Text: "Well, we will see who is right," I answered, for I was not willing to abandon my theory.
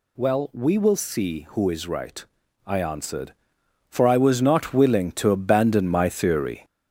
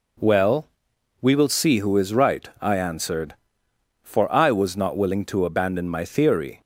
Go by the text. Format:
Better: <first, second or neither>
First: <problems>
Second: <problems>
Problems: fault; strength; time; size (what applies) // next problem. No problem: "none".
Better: second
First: gets louder; slight; throughout; 3 dB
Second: none